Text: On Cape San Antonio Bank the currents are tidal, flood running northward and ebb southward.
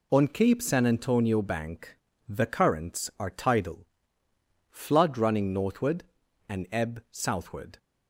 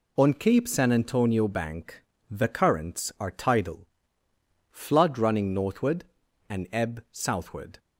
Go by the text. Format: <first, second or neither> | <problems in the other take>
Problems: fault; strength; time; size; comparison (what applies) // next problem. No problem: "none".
neither | pauses between "Bank" and "the"; slight; the same in both